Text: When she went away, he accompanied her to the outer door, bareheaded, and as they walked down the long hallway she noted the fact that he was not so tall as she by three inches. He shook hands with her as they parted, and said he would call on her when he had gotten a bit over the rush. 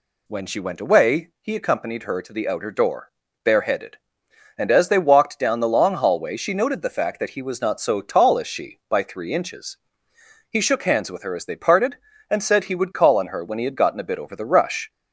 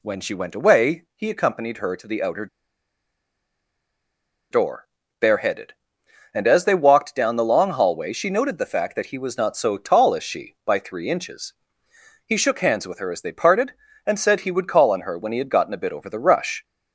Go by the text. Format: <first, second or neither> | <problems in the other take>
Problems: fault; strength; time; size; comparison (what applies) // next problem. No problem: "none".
first | pauses between "outer" and "door"; strong; at 2.4 s; 2.0 s long